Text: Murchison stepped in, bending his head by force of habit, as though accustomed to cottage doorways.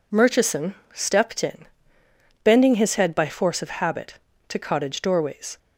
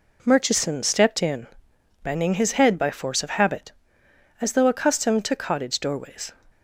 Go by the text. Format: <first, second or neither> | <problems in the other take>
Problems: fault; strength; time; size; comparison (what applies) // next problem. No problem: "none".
second | pauses between "Murchison" and "stepped"; slight; at 0.7 s; 0.18 s long // skips "as though accustomed"; at 4.3 s